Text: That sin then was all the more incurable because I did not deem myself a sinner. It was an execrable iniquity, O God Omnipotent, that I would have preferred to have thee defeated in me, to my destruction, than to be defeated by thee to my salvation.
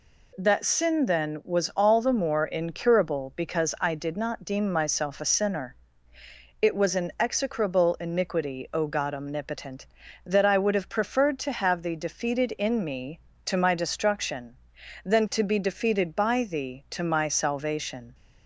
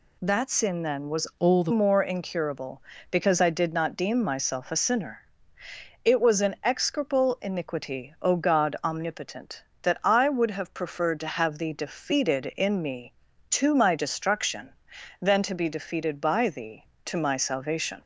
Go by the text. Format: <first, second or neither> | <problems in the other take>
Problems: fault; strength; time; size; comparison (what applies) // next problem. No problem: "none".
first | changes voice from "all" to "the"; from 1.3 to 1.7 s; 0.4 s long